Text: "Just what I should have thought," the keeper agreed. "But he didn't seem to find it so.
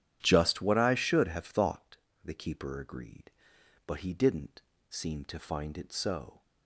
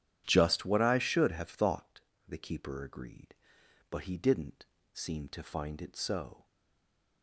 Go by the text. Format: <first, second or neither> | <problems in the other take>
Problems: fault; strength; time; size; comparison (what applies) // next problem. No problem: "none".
first | starts louder than the rest; strong; until 1.2 s; 10.5 dB; strong in the first // pauses between "didn't" and "seem"; slight; at 4.6 s; 0.26 s long; slight in the first // stays silent after the last word; slight; from 6.4 s on; 0.8 s long